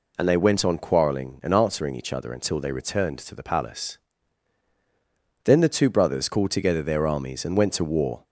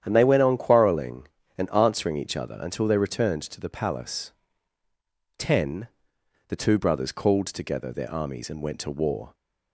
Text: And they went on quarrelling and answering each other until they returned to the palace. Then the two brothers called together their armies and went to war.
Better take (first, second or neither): first